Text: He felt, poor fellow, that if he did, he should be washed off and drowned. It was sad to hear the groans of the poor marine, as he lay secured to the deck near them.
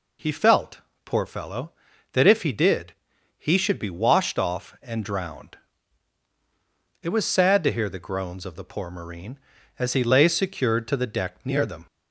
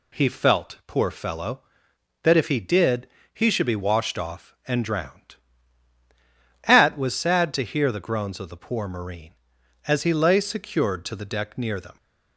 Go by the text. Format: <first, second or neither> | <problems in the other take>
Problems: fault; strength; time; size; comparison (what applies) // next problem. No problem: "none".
first | says "At" for "It"; at 6.6 s